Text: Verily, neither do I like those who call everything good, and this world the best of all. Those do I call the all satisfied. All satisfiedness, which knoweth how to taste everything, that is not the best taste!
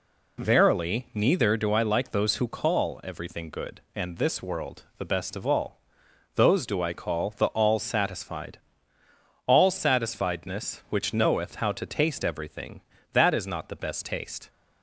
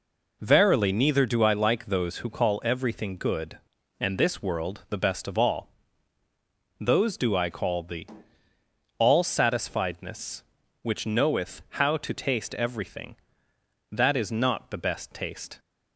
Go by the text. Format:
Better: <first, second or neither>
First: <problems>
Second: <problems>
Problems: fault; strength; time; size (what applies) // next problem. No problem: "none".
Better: first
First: none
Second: skips "all satisfied"; at 8.5 s